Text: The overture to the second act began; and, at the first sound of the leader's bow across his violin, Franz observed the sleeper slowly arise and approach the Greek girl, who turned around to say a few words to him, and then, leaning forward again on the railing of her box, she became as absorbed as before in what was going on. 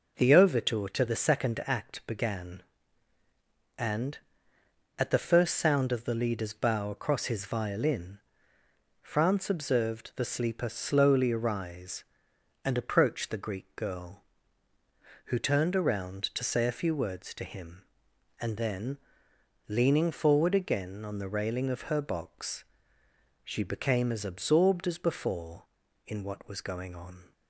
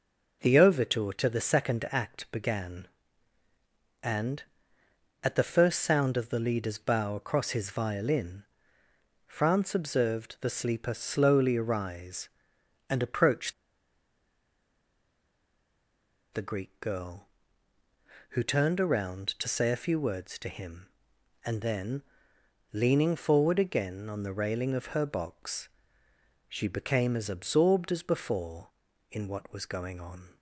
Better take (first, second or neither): first